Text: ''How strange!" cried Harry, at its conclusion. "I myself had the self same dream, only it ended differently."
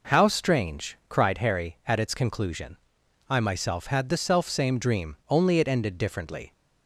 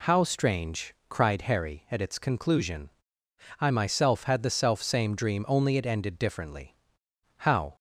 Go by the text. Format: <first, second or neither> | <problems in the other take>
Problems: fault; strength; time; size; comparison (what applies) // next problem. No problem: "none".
first | goes on to say "How"; slight; from 7.3 s on; 0.38 s long